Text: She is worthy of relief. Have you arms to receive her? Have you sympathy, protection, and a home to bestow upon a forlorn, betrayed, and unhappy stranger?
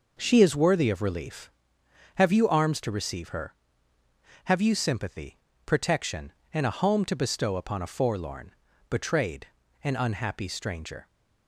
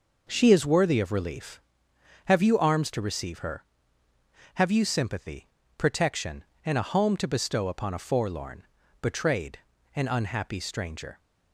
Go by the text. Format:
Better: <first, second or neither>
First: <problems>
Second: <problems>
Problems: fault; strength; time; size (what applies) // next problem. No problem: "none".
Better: neither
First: none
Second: none